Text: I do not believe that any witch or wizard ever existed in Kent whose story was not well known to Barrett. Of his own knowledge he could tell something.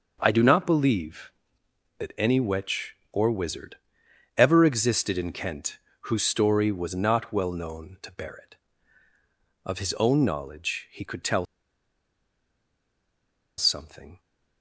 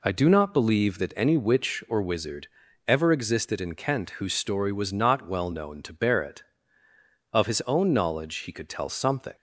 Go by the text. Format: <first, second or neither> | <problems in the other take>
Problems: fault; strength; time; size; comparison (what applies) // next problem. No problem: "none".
second | starts louder than the rest; until 1.2 s; 6 dB // pauses between "wizard" and "ever"; noticeable; at 3.7 s; 0.60 s long; also in the second // pauses between "Kent" and "whose"; slight; at 5.7 s; 0.24 s long // pauses between "tell" and "something"; strong; at 11.4 s; 2.1 s long